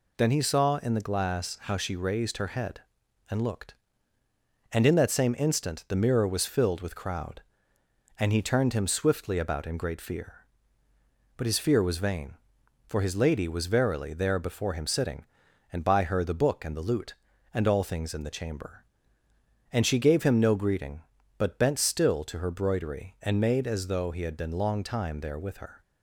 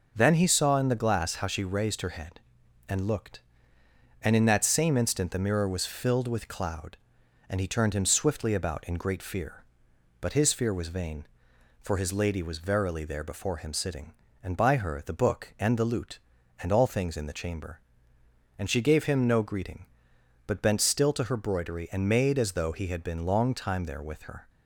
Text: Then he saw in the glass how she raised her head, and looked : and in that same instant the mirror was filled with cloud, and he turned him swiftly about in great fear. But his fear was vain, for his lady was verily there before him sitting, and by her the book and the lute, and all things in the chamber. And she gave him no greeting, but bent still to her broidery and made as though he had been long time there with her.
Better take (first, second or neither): second